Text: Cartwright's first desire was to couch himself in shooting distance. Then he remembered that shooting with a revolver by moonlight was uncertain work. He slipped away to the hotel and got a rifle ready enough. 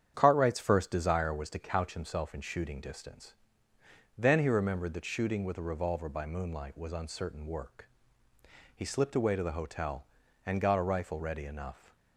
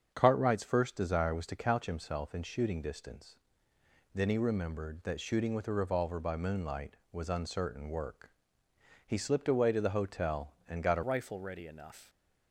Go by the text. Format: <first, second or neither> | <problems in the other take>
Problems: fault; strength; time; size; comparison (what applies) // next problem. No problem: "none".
first | starts louder than the rest; strong; until 1.1 s; 7 dB; strong in the first // changes voice at "rifle"; from 11.0 s on; 1.0 s long